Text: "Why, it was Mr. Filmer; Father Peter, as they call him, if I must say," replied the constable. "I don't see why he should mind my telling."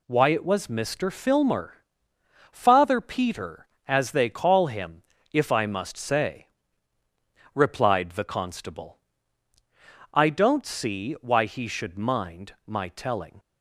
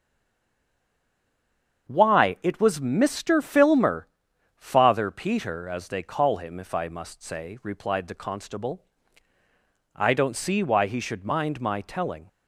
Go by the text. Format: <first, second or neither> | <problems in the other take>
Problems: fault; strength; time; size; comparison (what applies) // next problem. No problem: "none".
first | stays silent before the first word; noticeable; until 1.8 s; 1.8 s long // starts louder than the rest; strong; until 2.9 s; 7 dB